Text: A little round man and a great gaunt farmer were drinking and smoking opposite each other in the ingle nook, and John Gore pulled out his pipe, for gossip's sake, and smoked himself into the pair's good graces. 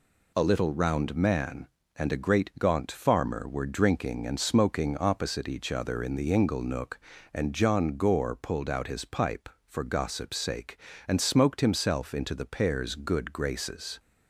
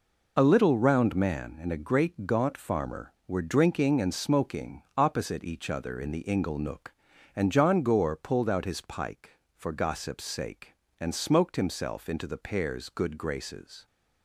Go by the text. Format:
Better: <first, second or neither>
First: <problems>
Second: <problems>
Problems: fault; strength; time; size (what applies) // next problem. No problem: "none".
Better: first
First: none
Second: says "pike" for "pipe"; at 8.7 s